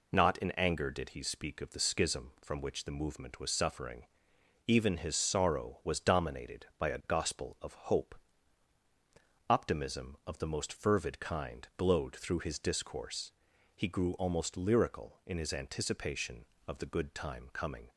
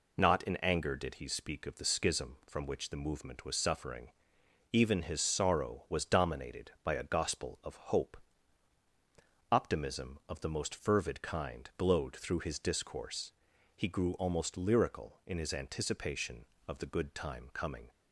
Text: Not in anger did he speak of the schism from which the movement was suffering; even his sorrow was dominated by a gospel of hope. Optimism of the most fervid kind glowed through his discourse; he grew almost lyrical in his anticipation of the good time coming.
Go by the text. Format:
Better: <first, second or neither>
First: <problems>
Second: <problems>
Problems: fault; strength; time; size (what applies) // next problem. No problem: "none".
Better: neither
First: none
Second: none